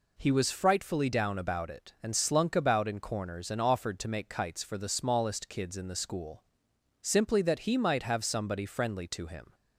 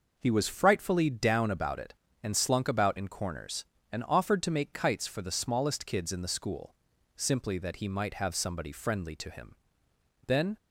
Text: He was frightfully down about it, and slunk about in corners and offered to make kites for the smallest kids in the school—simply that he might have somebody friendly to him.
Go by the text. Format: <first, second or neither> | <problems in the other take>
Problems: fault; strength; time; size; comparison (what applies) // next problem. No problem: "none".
first | goes on to say "Then"; slight; from 10.2 s on; 0.30 s long